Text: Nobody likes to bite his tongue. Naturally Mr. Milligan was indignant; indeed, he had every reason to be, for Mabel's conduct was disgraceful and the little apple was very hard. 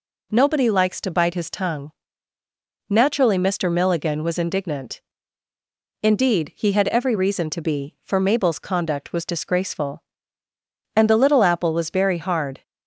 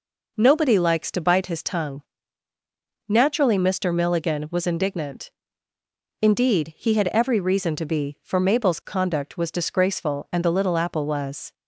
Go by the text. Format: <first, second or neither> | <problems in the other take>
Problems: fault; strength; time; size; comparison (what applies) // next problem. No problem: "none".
first | stops before "very hard"; at 11.5 s